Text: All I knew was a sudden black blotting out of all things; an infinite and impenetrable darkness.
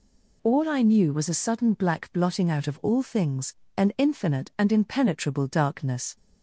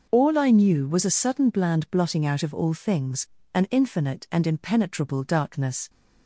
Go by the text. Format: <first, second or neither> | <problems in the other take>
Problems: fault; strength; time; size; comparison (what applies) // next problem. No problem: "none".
first | says "bland" for "black"; at 1.4 s